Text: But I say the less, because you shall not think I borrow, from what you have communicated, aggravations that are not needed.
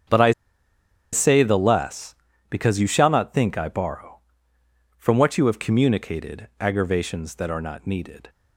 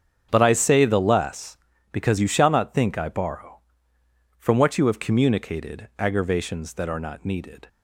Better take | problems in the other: second | starts louder than the rest; strong; until 1.9 s; 7.5 dB; strong in the second // pauses between "I" and "say"; noticeable; at 0.3 s; 0.81 s long

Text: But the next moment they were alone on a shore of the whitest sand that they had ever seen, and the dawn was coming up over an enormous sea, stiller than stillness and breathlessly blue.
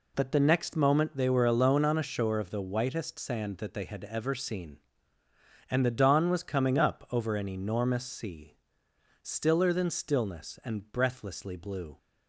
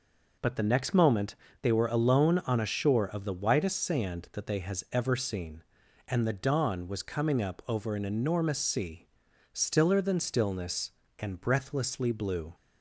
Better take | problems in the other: first | pauses between "moment" and "they"; slight; at 1.3 s; 0.26 s long // says "has" for "had"; at 4.5 s

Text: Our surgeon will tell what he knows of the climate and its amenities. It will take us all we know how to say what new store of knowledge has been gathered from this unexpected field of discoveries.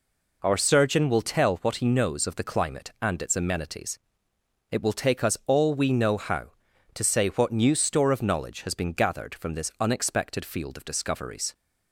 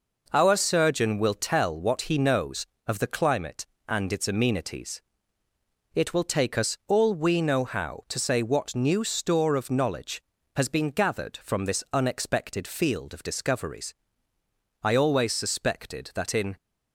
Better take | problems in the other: first | goes on to say "I always suspected that in"; strong; from 14.8 s on; 1.7 s long

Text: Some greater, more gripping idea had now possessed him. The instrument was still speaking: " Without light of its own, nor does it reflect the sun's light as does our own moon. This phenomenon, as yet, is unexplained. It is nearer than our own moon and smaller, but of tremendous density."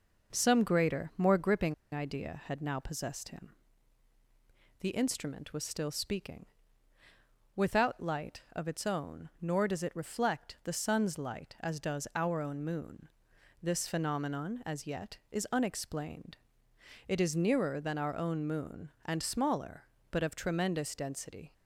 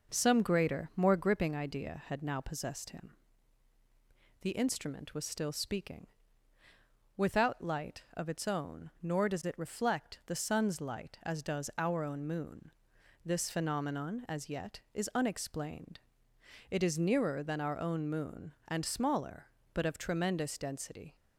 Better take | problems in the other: second | starts louder than the rest; noticeable; until 1.3 s; 6 dB; noticeable in the second // pauses between "gripping" and "idea"; slight; at 1.7 s; 0.18 s long

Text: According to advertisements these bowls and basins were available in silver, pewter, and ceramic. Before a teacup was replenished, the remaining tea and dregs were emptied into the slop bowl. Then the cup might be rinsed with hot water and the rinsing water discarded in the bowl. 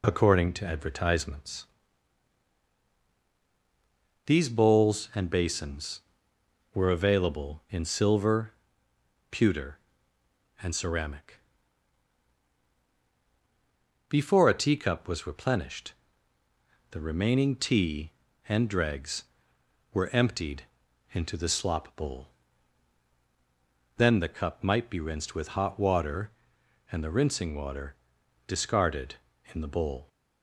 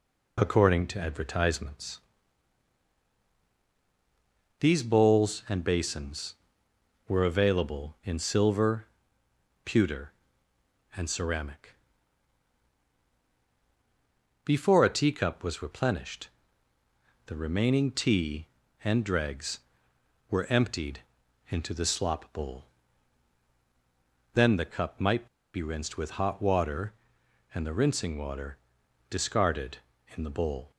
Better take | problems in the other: first | pauses between "advertisements" and "these"; strong; at 1.9 s; 2.6 s long; strong in the first // pauses between "emptied" and "into"; noticeable; at 21.0 s; 0.48 s long; noticeable in the first // pauses between "might" and "be"; slight; at 25.2 s; 0.27 s long // pauses between "water" and "discarded"; noticeable; at 28.5 s; 0.54 s long; noticeable in the first

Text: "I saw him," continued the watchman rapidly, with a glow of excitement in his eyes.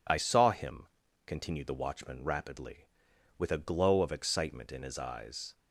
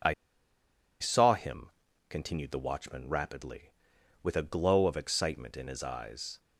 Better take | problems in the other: first | pauses between "I" and "saw"; noticeable; at 0.1 s; 0.89 s long

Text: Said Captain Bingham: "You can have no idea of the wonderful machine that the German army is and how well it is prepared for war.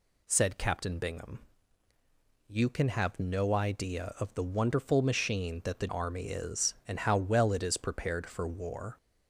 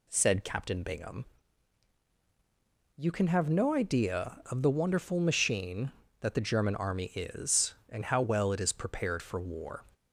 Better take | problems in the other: second | skips "German"; at 5.8 s

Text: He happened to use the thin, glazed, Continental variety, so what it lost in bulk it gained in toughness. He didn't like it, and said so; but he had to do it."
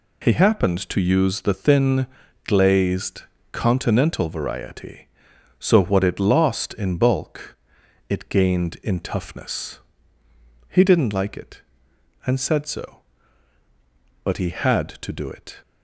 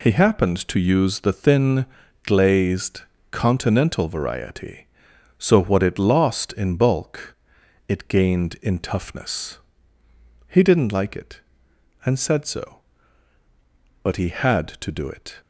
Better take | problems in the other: neither | pauses between "bulk" and "it"; noticeable; the same in both

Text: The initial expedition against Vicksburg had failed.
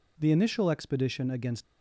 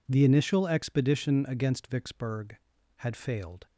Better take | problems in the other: second | stops before "Vicksburg had failed"; at 1.6 s

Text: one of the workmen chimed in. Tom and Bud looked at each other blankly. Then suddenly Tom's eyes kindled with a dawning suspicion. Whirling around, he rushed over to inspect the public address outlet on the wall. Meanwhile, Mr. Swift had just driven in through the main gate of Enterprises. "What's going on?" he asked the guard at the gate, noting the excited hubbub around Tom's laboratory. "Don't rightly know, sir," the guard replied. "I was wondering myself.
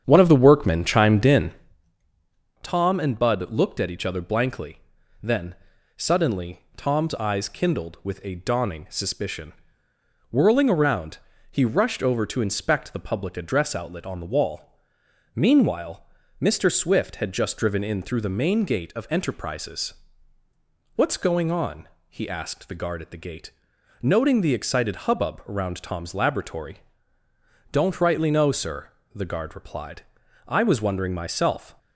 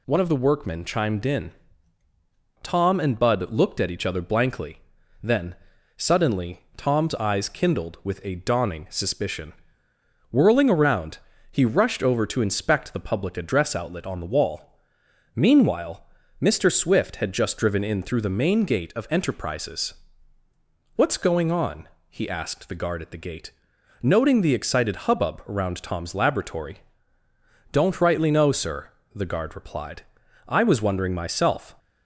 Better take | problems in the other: second | starts louder than the rest; strong; until 1.8 s; 8.5 dB // pauses between "Then" and "suddenly"; at 5.5 s; 0.42 s long; also in the second

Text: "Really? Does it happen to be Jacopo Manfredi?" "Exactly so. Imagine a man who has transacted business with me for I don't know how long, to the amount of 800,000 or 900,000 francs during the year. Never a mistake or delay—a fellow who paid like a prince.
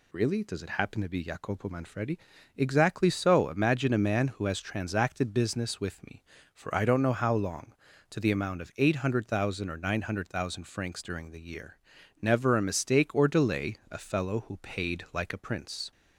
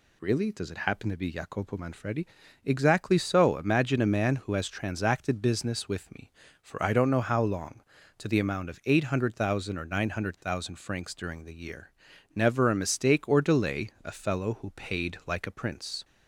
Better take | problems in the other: neither | none

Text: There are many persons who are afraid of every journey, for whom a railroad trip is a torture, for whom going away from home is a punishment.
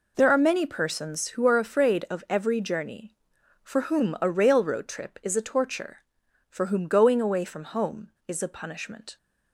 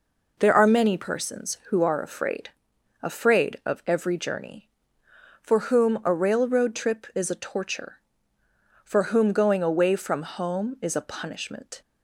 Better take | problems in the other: first | says "afraid" twice; at 3.0 s

